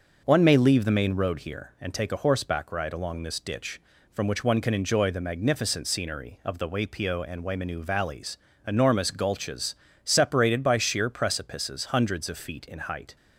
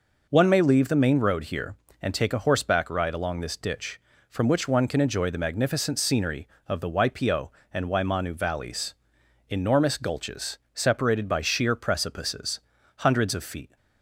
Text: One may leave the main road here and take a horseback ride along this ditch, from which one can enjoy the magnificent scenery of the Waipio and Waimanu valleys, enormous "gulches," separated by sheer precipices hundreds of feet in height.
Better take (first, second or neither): first